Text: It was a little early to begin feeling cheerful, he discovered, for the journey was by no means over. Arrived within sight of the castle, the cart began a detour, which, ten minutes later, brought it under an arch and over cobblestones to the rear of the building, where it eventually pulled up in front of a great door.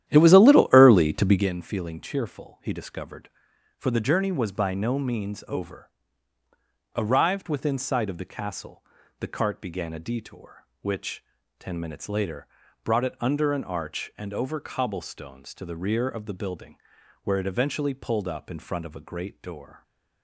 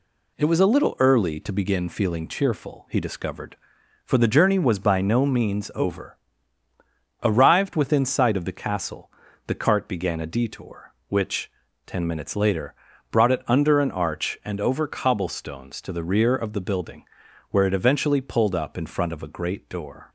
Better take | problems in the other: second | starts louder than the rest; strong; until 1.5 s; 11.5 dB

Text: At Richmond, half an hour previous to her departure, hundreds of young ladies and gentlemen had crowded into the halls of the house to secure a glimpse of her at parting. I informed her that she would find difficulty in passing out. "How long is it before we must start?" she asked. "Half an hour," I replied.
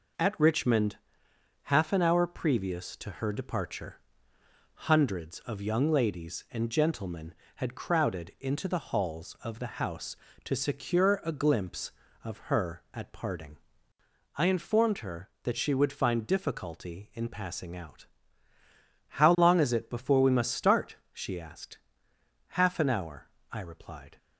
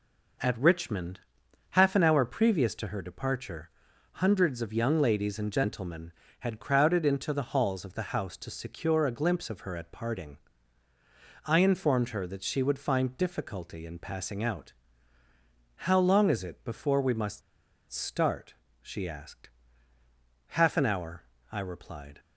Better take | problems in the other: first | pauses between "must" and "start"; noticeable; at 17.4 s; 0.50 s long

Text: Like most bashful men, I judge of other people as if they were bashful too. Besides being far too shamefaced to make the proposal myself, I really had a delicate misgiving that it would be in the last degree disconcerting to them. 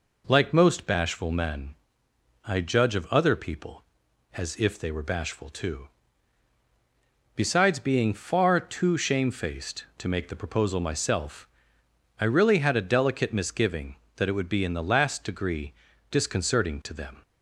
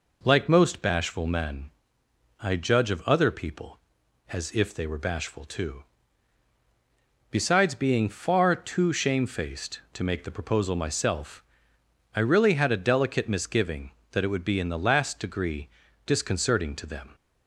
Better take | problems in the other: neither | pauses between "degree" and "disconcerting"; slight; the same in both

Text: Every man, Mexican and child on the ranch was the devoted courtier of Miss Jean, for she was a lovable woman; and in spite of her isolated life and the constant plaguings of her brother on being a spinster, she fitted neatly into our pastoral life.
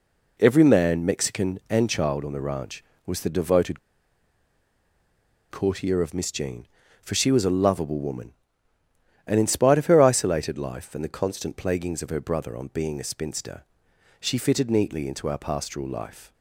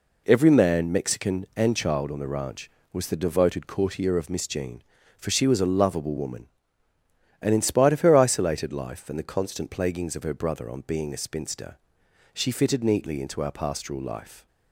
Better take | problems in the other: second | pauses between "devoted" and "courtier"; strong; at 3.7 s; 1.7 s long

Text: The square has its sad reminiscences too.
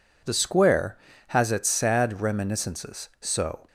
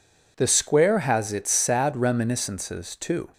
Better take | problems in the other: second | says "so" for "too"; at 3.1 s

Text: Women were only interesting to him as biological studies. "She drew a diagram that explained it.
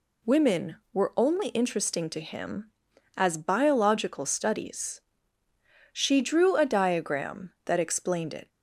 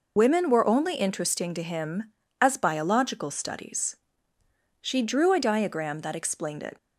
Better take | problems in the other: first | loses the start of "Women"; at 0.1 s; 85 ms

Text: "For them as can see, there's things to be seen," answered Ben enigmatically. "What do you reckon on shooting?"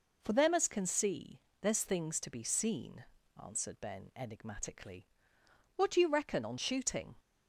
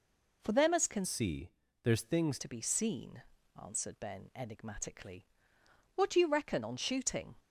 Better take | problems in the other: first | changes voice from "see" to "things"; from 1.0 to 2.3 s; 1.3 s long

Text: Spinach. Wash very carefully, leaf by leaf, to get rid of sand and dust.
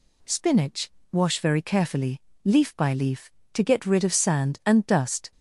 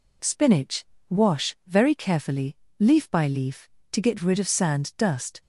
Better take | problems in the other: first | skips "and"; at 4.9 s

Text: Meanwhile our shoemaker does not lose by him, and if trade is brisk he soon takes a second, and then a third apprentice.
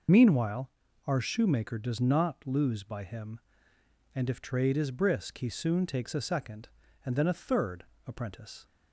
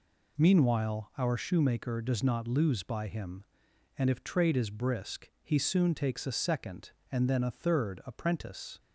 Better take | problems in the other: second | loses the start of "Meanwhile"; at 0.0 s; 35 ms // pauses between "Meanwhile" and "our"; slight; at 0.7 s; 0.36 s long // pauses between "third" and "apprentice"; slight; at 7.8 s; 0.24 s long

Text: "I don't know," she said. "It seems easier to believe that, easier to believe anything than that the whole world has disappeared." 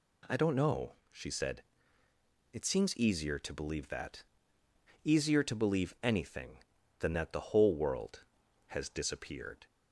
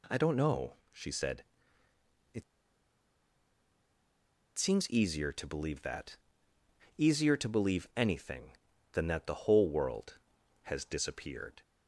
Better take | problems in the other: first | pauses between "It" and "seems"; strong; at 2.4 s; 2.1 s long

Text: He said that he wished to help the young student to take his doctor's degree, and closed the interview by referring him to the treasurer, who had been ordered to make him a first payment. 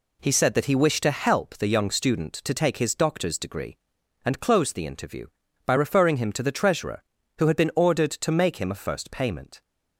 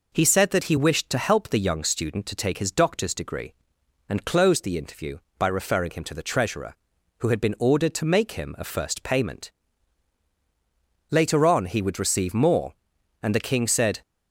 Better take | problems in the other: first | goes on to say "Later on he would receive more and the king said"; strong; from 11.0 s on; 2.9 s long

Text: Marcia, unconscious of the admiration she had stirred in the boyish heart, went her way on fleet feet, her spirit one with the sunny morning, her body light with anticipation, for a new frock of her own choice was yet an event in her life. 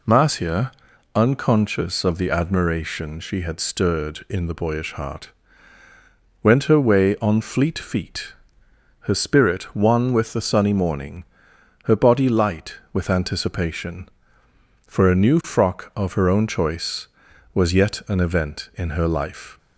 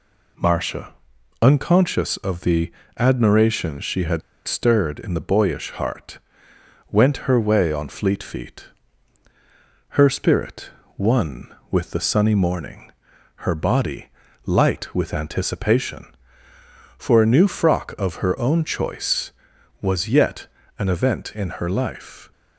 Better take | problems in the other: first | pauses between "the" and "admiration"; slight; at 2.7 s; 0.26 s long // pauses between "had" and "stirred"; slight; at 4.2 s; 0.25 s long // pauses between "spirit" and "one"; slight; at 10.7 s; 0.24 s long // pauses between "body" and "light"; at 14.0 s; 0.38 s long // pauses between "yet" and "an"; slight; at 20.4 s; 0.32 s long

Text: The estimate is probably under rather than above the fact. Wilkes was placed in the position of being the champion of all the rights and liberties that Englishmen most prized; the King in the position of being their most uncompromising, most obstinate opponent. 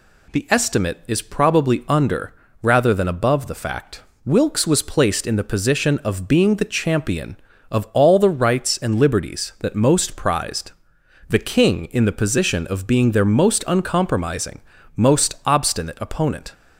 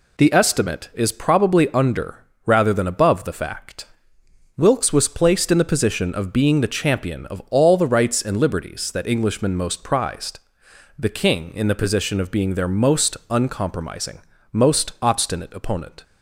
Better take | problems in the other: second | pauses between "under" and "rather"; slight; at 2.3 s; 0.26 s long; slight in the second // skips "Englishmen"; at 9.7 s

